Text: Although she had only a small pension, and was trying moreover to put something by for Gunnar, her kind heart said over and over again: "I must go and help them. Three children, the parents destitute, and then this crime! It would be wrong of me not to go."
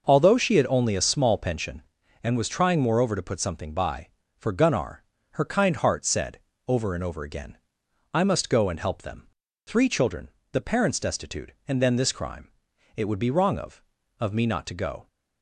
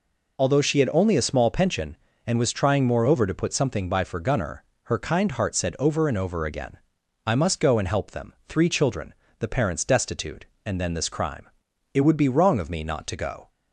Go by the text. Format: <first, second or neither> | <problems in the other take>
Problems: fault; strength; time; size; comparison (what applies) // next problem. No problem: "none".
second | pauses between "said" and "over"; slight; at 6.3 s; 0.28 s long // says "of" twice; at 14.1 s